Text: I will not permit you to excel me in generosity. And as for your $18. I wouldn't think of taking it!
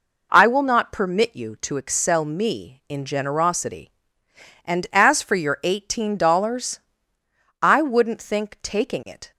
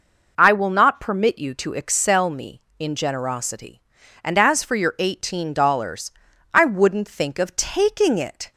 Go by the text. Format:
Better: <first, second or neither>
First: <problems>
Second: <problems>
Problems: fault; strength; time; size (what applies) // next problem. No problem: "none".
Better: second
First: skips "of"; at 8.5 s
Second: none